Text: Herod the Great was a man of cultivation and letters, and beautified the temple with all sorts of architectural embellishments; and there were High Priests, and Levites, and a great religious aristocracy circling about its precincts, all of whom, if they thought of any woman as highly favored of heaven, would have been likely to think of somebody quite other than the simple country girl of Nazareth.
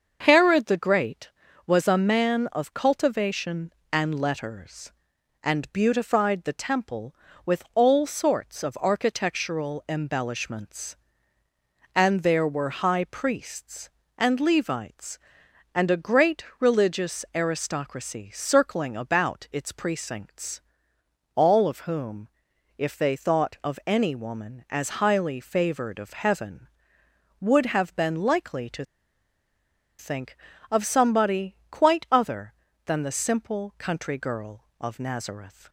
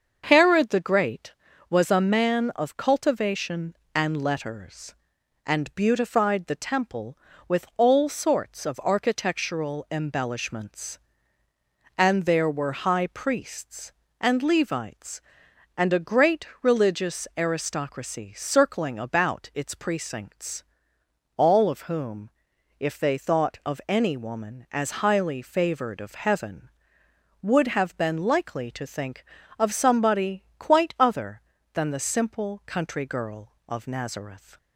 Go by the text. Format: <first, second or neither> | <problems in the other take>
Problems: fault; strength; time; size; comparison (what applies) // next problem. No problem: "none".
second | starts louder than the rest; until 1.2 s; 6.5 dB; also in the second // pauses between "to" and "think"; at 28.8 s; 1.1 s long